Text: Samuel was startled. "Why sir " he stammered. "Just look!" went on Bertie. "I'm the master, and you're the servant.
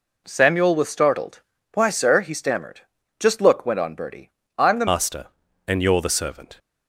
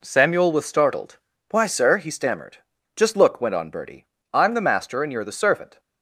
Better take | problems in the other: second | changes voice at "master"; from 4.8 s on; 1.7 s long

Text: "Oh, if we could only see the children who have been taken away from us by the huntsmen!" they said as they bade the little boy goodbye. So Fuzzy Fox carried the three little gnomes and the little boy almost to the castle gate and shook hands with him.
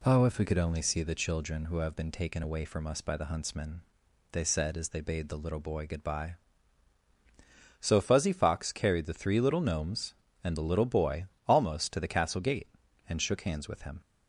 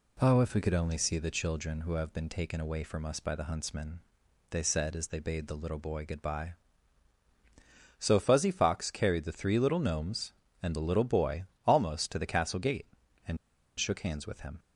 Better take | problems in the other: first | pauses between "boy" and "almost"; slight; at 11.4 s; 0.24 s long; slight in the first // pauses between "and" and "shook"; at 13.3 s; 0.42 s long

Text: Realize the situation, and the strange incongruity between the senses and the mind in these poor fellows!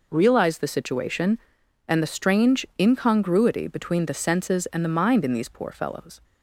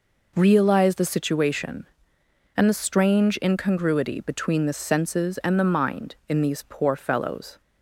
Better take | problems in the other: neither | none

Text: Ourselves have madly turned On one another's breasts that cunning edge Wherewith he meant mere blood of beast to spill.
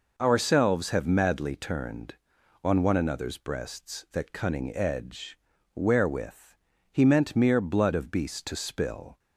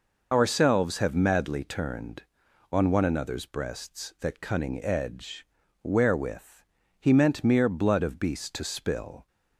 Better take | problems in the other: first | loses the start of "Ourselves"; at 0.3 s; 45 ms // pauses between "edge" and "Wherewith"; at 5.4 s; 0.38 s long; also in the first // pauses between "Wherewith" and "he"; slight; at 6.6 s; 0.34 s long; slight in the first

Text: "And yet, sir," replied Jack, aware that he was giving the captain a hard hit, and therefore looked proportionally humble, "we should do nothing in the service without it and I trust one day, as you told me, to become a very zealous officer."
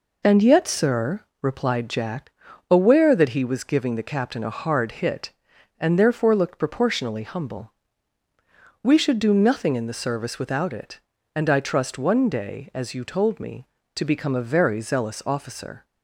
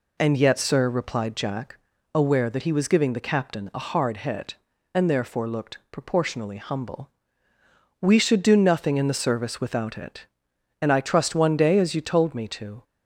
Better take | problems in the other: first | stops before "become a very zealous officer"; at 12.8 s

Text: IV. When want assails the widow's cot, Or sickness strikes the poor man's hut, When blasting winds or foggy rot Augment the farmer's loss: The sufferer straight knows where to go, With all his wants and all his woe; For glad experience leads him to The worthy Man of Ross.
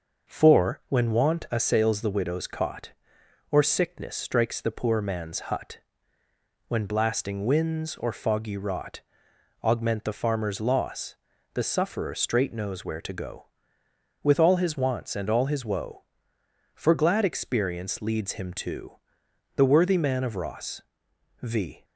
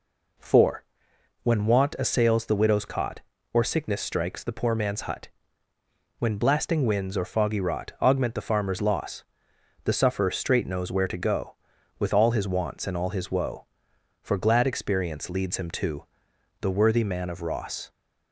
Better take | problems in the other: second | pauses between "rot" and "Augment"; noticeable; at 8.9 s; 0.64 s long // pauses between "to" and "The"; noticeable; at 18.9 s; 0.60 s long; noticeable in the second // goes on to say "V"; slight; from 21.3 s on; 0.44 s long

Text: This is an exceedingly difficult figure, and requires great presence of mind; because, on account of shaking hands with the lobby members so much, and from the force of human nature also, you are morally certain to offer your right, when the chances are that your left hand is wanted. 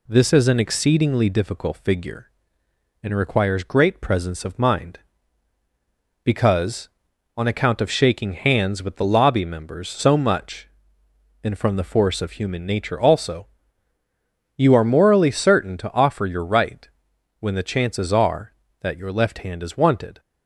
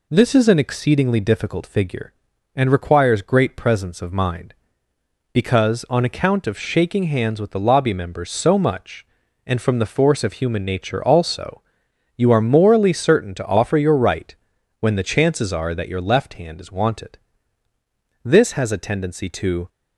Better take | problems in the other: first | goes on to say "This has a tendency to"; from 18.2 s on; 1.4 s long

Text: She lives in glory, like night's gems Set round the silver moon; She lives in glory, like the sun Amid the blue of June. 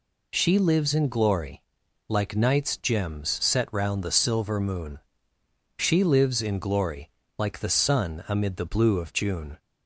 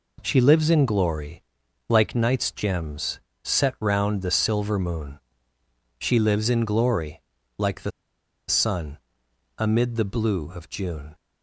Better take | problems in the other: first | pauses between "gems" and "Set"; slight; at 3.1 s; 0.22 s long // pauses between "the" and "sun"; noticeable; at 7.9 s; 0.58 s long // pauses between "sun" and "Amid"; noticeable; at 8.9 s; 0.58 s long

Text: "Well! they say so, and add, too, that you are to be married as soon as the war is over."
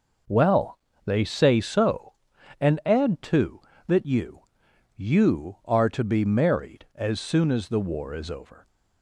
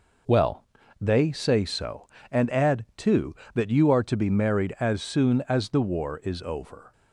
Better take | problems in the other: second | says "you" twice; at 4.9 s

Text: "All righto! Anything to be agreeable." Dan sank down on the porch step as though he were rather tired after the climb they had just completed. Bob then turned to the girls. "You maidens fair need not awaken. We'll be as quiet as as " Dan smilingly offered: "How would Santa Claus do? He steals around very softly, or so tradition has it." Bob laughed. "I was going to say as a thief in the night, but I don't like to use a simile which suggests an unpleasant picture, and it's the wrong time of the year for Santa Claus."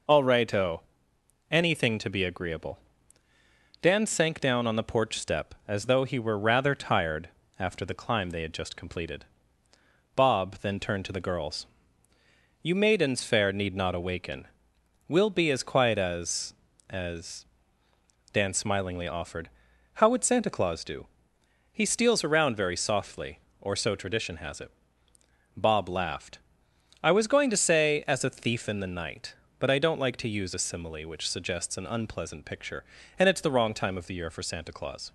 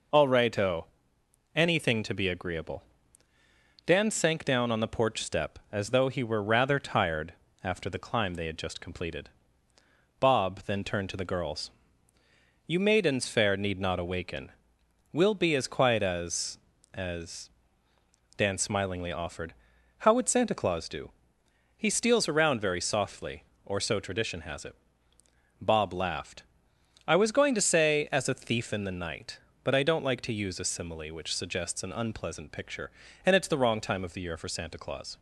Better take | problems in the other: neither | pauses between "tired" and "after"; slight; the same in both

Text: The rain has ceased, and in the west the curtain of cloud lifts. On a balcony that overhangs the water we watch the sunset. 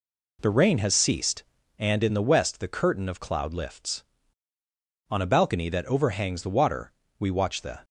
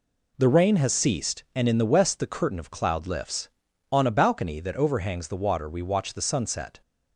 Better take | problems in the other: second | pauses between "water" and "we"; slight; at 6.9 s; 0.26 s long // stops before "sunset"; at 7.8 s

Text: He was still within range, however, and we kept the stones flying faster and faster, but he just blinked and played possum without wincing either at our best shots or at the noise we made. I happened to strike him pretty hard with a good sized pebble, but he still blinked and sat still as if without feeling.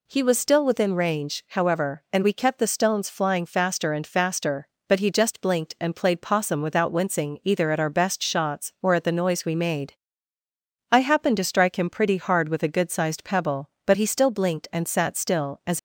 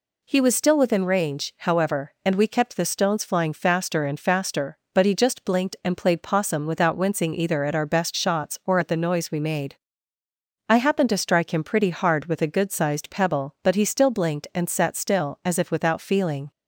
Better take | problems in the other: second | stops before "if without feeling"; at 15.7 s

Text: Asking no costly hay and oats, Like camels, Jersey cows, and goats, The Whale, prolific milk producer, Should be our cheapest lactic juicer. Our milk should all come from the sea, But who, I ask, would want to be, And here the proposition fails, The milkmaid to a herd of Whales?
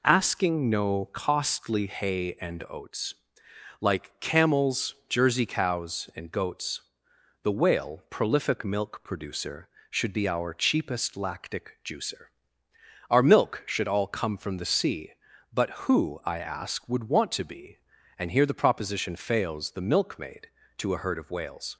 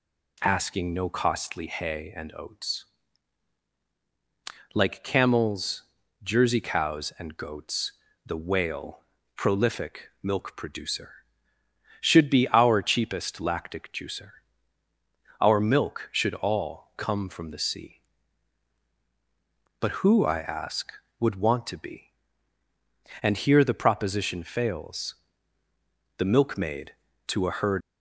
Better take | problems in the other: first | stops before "of Whales"; at 27.8 s

